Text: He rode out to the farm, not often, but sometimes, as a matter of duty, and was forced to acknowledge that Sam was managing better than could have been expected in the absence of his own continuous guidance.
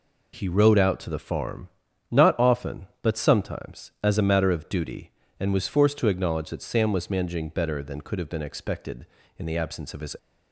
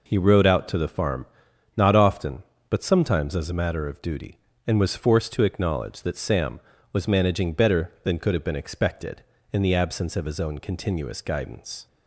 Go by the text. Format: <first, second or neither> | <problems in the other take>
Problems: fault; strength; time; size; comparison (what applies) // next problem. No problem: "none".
second | stops before "own continuous guidance"; at 10.1 s